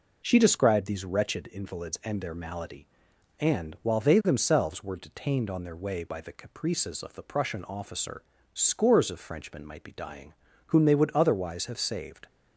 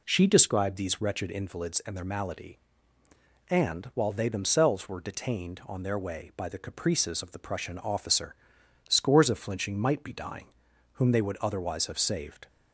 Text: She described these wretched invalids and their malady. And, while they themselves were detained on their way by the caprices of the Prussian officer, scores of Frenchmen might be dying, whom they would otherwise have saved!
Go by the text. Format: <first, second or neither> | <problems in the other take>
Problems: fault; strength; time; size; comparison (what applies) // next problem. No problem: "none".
first | says "Flinching" for "Frenchmen"; at 9.3 s